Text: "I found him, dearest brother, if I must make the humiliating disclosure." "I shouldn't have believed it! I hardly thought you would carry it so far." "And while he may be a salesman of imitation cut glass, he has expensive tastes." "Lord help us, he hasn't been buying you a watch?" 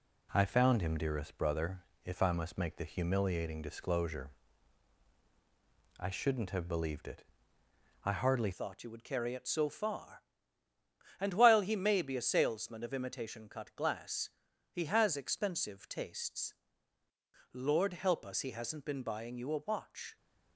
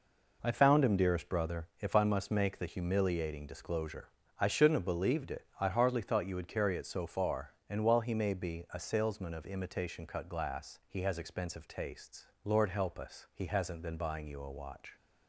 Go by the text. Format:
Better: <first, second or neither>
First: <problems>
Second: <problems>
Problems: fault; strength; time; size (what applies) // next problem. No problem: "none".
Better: second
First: changes voice at "thought"; from 8.5 s on; 11.6 s long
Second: none